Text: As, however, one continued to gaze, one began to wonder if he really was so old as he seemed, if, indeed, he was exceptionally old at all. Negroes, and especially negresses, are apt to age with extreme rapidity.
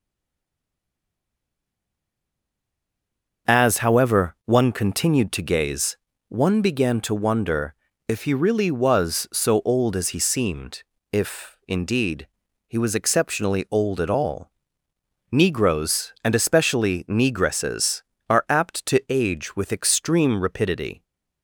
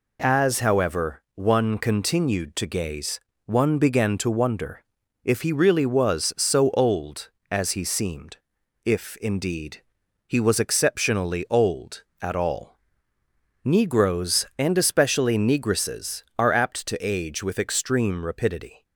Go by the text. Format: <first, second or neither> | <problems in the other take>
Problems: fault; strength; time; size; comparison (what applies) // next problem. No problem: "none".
second | stays silent before the first word; strong; until 3.4 s; 3.4 s long // starts louder than the rest; until 4.5 s; 6.5 dB // pauses between "wonder" and "if"; slight; at 7.7 s; 0.32 s long; also in the second